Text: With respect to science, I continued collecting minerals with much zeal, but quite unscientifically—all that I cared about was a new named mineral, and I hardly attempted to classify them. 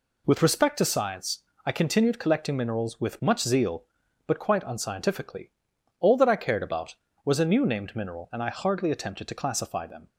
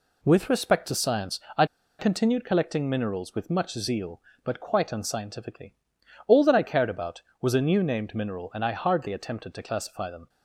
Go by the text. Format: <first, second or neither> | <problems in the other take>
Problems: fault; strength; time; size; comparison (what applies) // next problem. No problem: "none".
first | pauses between "I" and "continued"; slight; at 1.6 s; 0.33 s long